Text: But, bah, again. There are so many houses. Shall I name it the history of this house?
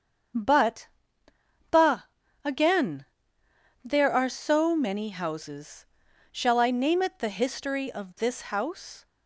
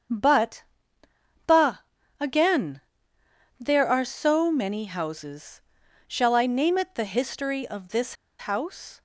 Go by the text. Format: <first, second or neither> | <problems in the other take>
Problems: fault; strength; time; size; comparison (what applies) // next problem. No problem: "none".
first | starts louder than the rest; until 2.3 s; 7 dB; also in the first // pauses between "this" and "house"; slight; at 8.1 s; 0.25 s long